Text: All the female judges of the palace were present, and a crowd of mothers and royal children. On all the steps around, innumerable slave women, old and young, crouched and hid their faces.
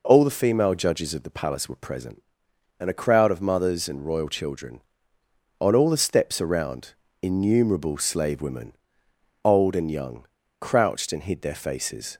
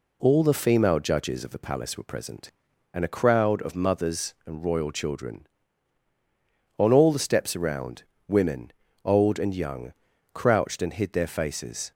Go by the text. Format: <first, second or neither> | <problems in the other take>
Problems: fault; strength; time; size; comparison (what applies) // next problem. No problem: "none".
first | skips "innumerable slave"; at 8.1 s